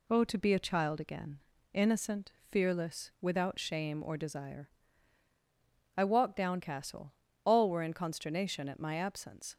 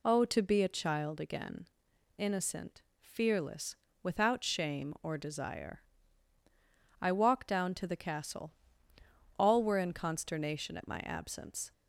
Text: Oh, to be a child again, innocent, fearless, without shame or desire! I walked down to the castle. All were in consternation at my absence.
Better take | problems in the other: second | skips "to the"; at 6.6 s

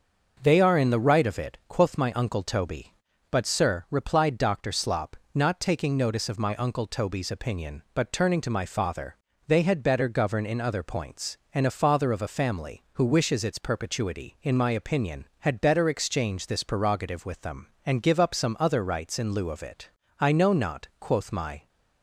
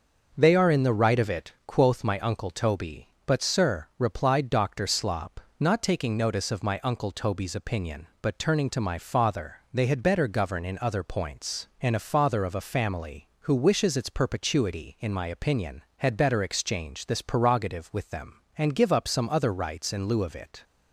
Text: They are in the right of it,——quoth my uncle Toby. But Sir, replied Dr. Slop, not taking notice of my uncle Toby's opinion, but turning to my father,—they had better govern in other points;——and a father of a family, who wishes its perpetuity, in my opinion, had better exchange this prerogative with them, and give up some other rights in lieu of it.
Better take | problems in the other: second | starts louder than the rest; noticeable; until 1.4 s; 6 dB; also in the second // goes on to say "I know not quoth my"; from 20.1 s on; 1.4 s long

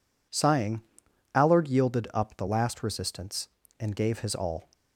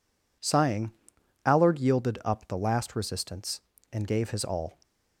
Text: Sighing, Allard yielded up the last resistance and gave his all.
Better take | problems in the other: neither | none

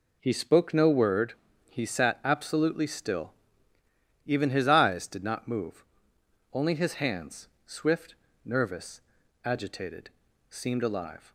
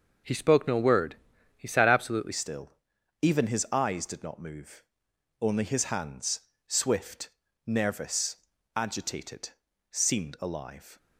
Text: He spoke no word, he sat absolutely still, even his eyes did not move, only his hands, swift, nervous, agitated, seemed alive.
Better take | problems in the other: first | changes voice at "still"; from 2.3 s on; 8.6 s long

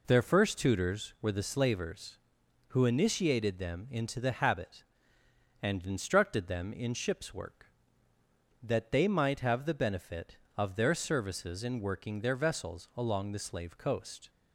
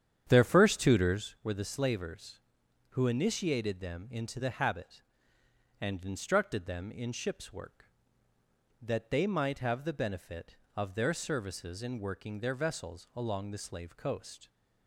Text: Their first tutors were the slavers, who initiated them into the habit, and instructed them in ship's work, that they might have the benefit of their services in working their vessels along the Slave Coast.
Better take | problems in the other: first | starts louder than the rest; strong; until 1.3 s; 9 dB

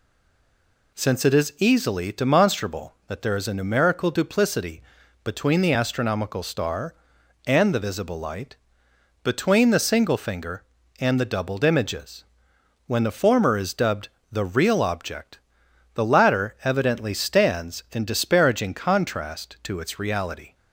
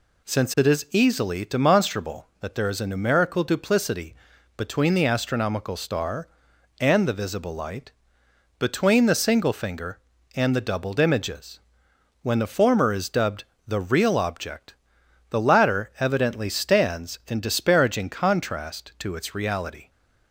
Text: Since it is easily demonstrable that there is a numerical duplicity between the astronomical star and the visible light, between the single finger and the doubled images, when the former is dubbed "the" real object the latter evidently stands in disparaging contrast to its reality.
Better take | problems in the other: second | stays silent before the first word; slight; until 0.9 s; 0.9 s long // pauses between "duplicity" and "between"; at 4.8 s; 0.42 s long; also in the second // pauses between "dubbed" and "the"; slight; at 14.0 s; 0.24 s long; slight in the second // pauses between "object" and "the"; noticeable; at 15.3 s; 0.56 s long; noticeable in the second

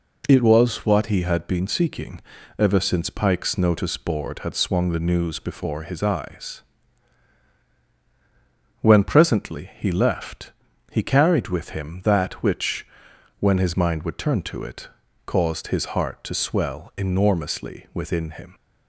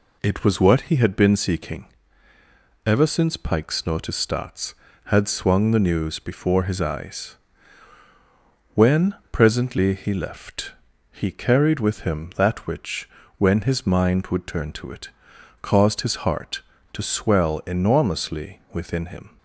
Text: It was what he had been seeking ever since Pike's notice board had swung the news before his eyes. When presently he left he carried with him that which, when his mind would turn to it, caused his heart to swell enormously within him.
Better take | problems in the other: first | pauses between "seeking" and "ever"; noticeable; at 1.8 s; 0.98 s long; also in the first // says "starts" for "board"; at 4.1 s // pauses between "When" and "presently"; slight; at 9.1 s; 0.16 s long // pauses between "left" and "he"; at 10.7 s; 0.40 s long; also in the first

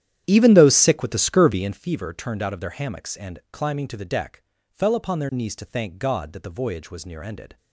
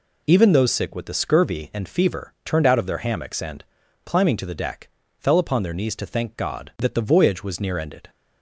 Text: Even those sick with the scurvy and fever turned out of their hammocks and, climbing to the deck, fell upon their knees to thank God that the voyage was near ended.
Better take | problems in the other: second | starts louder than the rest; strong; until 1.8 s; 11 dB

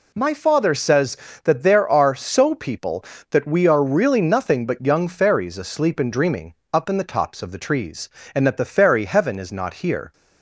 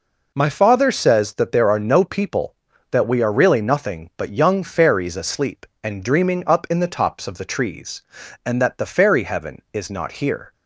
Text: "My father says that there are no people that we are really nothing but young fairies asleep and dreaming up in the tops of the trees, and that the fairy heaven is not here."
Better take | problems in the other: second | says "so" for "no"; at 2.1 s // pauses between "dreaming" and "up"; slight; at 6.5 s; 0.18 s long

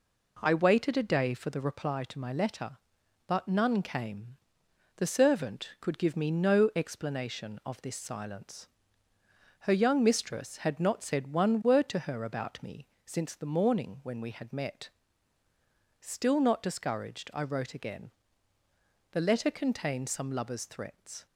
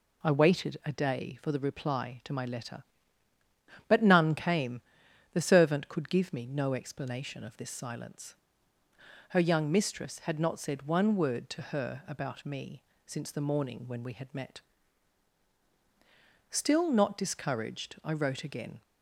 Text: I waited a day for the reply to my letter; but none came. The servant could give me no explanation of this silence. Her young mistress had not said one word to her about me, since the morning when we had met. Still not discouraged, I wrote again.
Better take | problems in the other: second | goes on to say "The letter contained some lover's threats"; strong; from 19.1 s on; 2.1 s long

